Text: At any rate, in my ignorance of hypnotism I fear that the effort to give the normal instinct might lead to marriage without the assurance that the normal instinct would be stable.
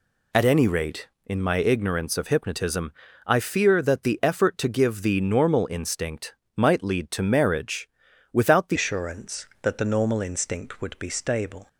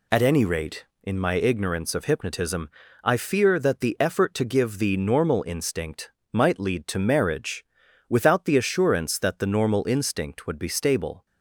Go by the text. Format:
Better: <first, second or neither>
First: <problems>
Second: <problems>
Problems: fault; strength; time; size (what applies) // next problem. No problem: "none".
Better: second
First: pauses between "hypnotism" and "I"; slight; at 2.9 s; 0.34 s long // pauses between "instinct" and "might"; slight; at 6.3 s; 0.20 s long // pauses between "marriage" and "without"; at 7.8 s; 0.42 s long // changes voice at "assurance"; from 8.7 s on; 2.9 s long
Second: pauses between "hypnotism" and "I"; slight; at 2.6 s; 0.34 s long // pauses between "instinct" and "might"; slight; at 6.1 s; 0.20 s long // pauses between "marriage" and "without"; at 7.6 s; 0.42 s long